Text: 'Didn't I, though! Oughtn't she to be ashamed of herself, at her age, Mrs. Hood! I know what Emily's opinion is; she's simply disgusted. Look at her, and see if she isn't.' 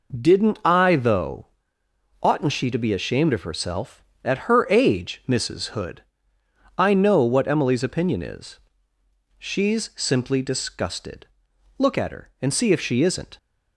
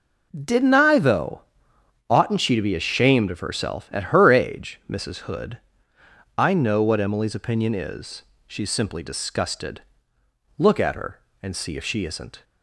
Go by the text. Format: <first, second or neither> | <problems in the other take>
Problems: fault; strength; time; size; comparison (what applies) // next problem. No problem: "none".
neither | none